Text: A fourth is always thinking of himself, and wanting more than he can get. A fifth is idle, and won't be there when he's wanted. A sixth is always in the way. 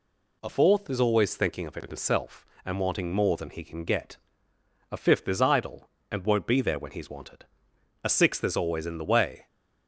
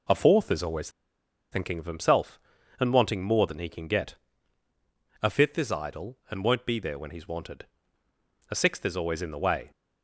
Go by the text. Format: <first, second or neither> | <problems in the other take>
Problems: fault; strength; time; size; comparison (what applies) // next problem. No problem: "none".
first | pauses between "always" and "thinking"; noticeable; at 0.8 s; 0.63 s long